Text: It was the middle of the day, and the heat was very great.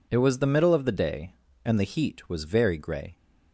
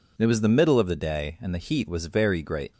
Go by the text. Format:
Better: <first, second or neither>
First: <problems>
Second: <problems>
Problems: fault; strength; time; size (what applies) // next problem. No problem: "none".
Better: second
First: says "grey" for "great"; at 2.7 s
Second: none